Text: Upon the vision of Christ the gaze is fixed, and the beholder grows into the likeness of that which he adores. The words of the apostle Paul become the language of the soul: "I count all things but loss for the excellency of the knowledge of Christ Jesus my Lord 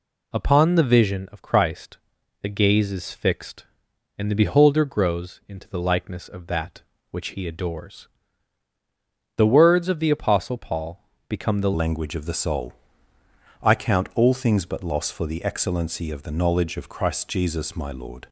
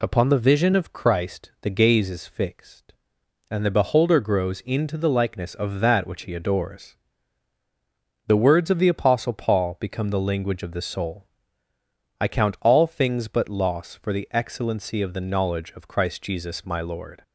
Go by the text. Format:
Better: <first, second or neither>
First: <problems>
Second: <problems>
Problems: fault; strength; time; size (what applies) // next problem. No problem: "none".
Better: second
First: pauses between "Christ" and "the"; at 1.9 s; 0.44 s long // pauses between "Paul" and "become"; slight; at 11.0 s; 0.24 s long // changes voice at "language"; from 11.7 s on; 6.5 s long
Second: none